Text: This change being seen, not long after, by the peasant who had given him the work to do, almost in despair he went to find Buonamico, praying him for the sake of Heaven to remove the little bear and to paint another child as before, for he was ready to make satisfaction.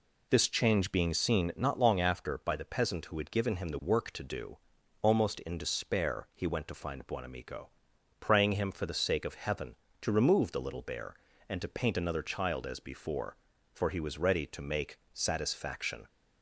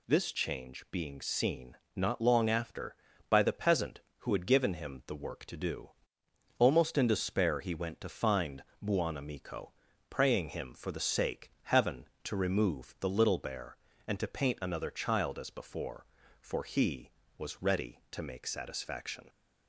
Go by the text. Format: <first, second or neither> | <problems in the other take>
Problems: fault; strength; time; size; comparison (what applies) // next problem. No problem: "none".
first | pauses between "find" and "Buonamico"; slight; at 8.6 s; 0.20 s long // skips "of"; at 11.5 s